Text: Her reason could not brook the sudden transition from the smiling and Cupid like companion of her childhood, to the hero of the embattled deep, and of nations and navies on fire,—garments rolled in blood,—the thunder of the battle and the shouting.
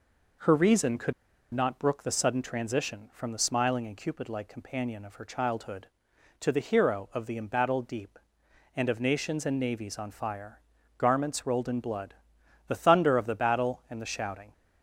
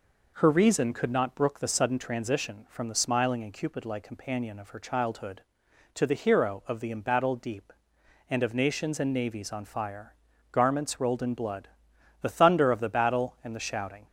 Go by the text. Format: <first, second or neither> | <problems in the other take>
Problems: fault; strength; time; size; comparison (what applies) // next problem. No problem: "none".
second | pauses between "could" and "not"; at 1.1 s; 0.41 s long